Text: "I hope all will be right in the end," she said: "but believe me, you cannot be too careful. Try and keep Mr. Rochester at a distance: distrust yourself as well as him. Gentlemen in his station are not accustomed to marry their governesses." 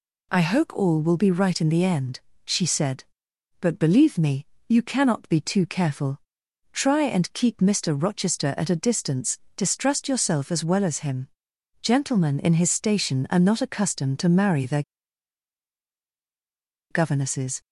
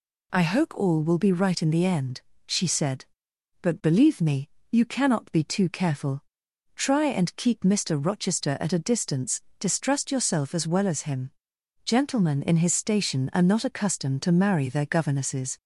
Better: second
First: pauses between "their" and "governesses"; strong; at 14.8 s; 2.0 s long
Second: none

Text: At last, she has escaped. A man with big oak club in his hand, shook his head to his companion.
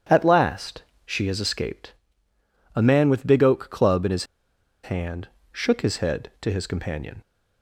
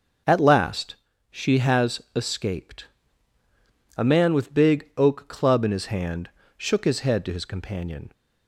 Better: second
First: starts louder than the rest; strong; until 1.3 s; 9 dB // pauses between "his" and "hand"; noticeable; at 4.2 s; 0.58 s long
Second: starts louder than the rest; noticeable; until 1.6 s; 6 dB

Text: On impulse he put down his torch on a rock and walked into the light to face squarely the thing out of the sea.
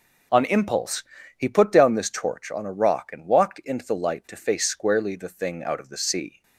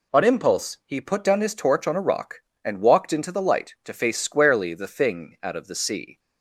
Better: second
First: pauses between "impulse" and "he"; slight; at 1.0 s; 0.36 s long // says "this" for "his"; at 1.9 s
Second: none

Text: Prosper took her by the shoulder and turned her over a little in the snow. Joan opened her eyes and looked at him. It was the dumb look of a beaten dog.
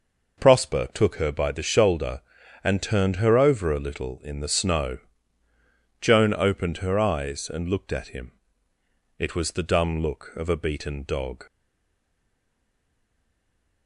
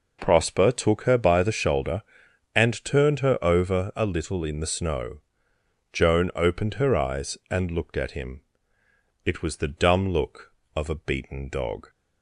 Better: second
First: stays silent after the last word; from 11.4 s on; 2.4 s long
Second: none

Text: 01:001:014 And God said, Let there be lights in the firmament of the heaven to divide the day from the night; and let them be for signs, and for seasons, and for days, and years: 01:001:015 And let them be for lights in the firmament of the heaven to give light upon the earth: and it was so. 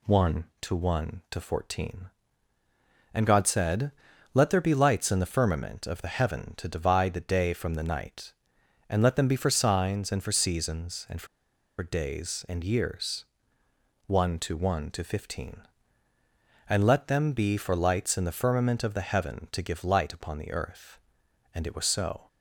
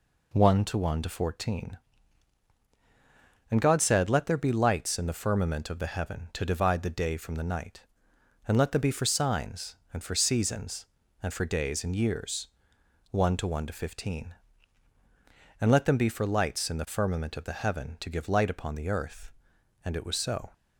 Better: second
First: pauses between "for" and "days"; noticeable; at 11.2 s; 0.54 s long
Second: none

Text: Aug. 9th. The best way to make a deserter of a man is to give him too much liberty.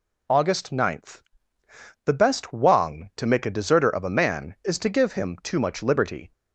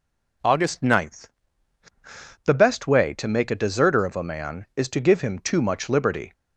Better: second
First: says "wang" for "way"; at 2.5 s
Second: none

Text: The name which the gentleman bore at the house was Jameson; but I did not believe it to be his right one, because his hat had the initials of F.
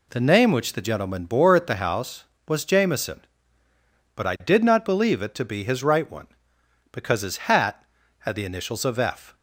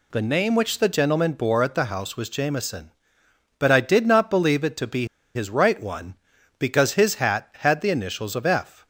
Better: first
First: none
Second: pauses between "be" and "his"; slight; at 5.0 s; 0.27 s long

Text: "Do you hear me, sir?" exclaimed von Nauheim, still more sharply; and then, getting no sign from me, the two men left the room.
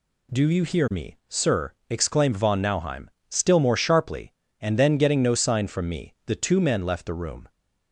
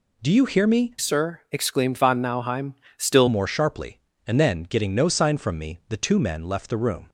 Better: first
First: none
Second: changes voice from "sir" to "still"; from 0.9 to 3.2 s; 2.3 s long

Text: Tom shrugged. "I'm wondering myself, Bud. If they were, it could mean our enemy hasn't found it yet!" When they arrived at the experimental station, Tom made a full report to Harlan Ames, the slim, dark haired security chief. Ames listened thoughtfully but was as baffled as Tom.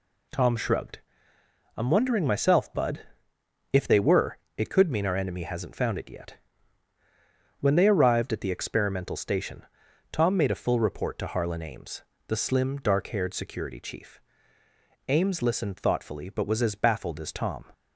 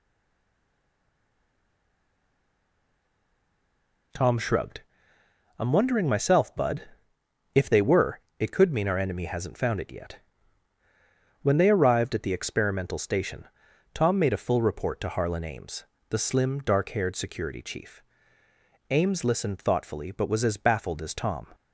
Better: first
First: none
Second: stays silent before the first word; strong; until 4.1 s; 4.1 s long

